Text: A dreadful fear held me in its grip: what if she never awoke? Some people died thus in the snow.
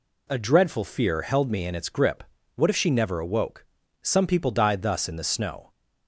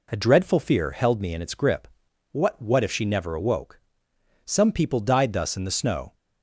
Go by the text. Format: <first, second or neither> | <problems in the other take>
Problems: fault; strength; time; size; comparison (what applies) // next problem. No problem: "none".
first | says "what" twice; at 2.5 s